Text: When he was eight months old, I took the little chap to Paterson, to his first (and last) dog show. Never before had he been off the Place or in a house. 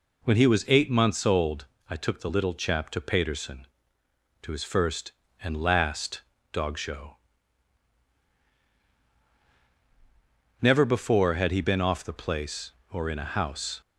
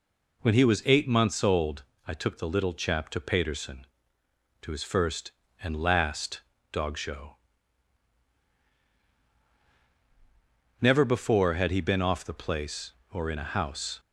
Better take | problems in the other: neither | none

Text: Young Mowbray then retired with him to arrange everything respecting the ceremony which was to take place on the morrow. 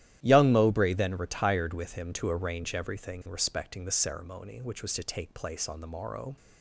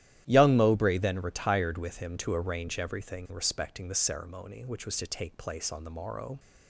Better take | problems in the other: neither | starts louder than the rest; strong; the same in both

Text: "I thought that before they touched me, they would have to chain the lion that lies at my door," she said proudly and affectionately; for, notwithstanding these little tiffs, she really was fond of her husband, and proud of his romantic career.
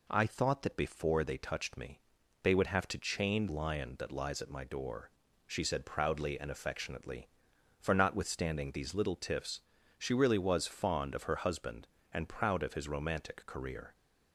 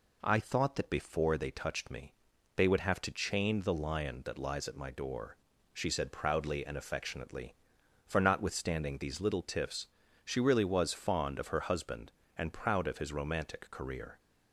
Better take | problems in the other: second | skips "the"; at 3.4 s

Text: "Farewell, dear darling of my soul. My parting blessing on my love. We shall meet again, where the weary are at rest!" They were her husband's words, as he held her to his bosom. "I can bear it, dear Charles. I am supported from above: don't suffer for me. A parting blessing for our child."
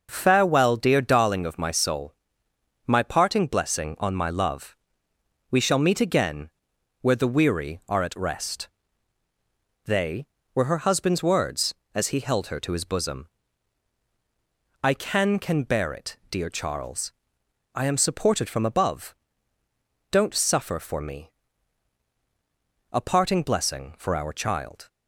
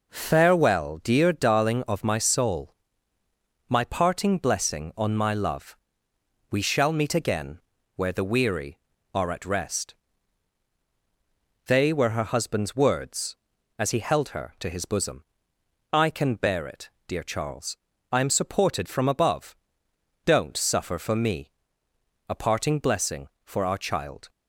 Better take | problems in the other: second | says "can" twice; at 15.3 s

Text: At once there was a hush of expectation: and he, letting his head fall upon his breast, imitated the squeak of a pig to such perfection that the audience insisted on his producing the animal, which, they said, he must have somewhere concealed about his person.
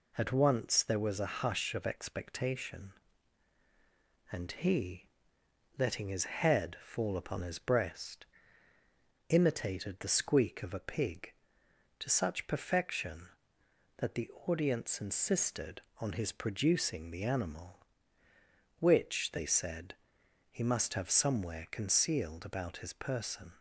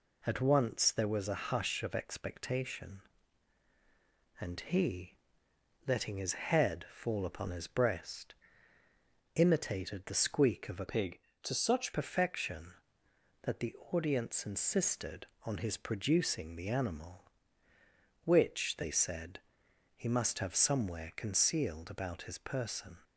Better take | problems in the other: first | changes voice from "pig" to "such"; from 10.8 to 11.9 s; 1.1 s long // pauses between "the" and "audience"; slight; at 13.7 s; 0.18 s long; slight in the first

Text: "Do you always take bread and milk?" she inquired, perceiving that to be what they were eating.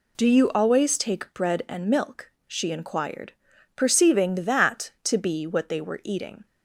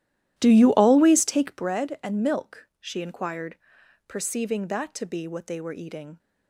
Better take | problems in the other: first | starts louder than the rest; strong; until 1.6 s; 13 dB

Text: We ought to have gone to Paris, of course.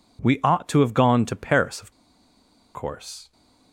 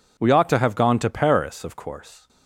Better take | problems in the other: second | pauses between "of" and "course"; noticeable; at 1.9 s; 0.82 s long

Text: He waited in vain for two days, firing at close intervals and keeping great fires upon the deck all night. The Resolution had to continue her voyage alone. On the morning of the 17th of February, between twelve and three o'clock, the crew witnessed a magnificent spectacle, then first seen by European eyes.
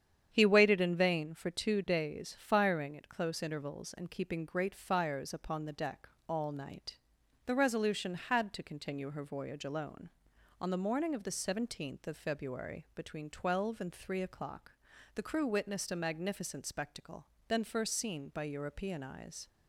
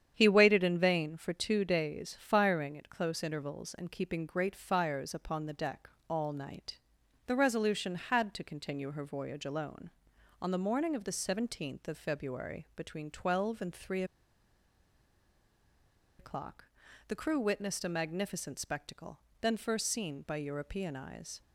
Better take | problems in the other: first | starts louder than the rest; strong; until 1.1 s; 9 dB; strong in the first // pauses between "deck" and "all"; slight; at 5.8 s; 0.20 s long; slight in the first // pauses between "three" and "o'clock"; strong; at 14.0 s; 2.1 s long

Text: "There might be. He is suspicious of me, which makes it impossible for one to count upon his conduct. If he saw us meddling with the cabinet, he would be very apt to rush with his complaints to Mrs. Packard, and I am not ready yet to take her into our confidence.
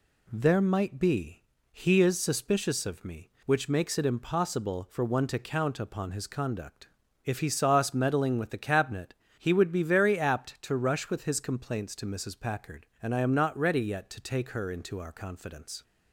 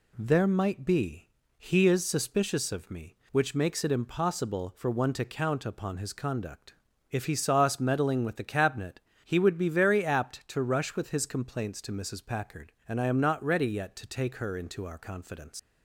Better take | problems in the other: first | leaves "confidence" unfinished; at 15.5 s; 85 ms

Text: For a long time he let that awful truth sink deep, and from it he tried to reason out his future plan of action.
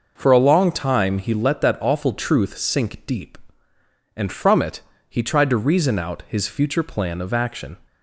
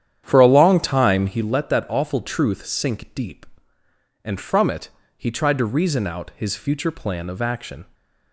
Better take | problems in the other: first | starts louder than the rest; strong; until 1.4 s; 9.5 dB // pauses between "it" and "he"; slight; at 4.8 s; 0.30 s long; slight in the first

